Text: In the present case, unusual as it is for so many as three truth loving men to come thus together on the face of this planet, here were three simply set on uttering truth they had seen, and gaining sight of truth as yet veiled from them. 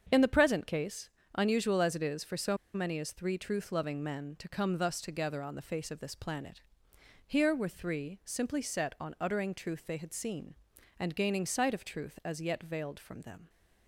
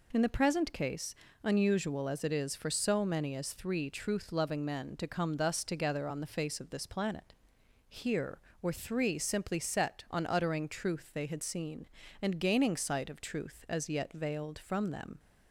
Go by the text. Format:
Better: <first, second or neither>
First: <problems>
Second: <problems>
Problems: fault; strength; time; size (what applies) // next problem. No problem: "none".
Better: second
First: starts louder than the rest; strong; until 1.1 s; 7.5 dB // pauses between "so" and "many"; slight; at 2.5 s; 0.18 s long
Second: none